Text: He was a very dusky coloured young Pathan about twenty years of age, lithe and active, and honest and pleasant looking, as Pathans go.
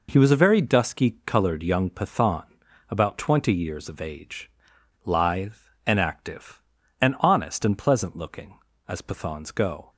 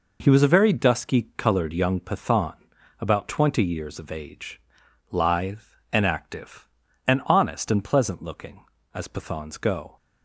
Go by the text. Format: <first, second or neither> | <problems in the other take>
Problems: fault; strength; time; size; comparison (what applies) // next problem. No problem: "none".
neither | pauses between "Pathan" and "about"; noticeable; the same in both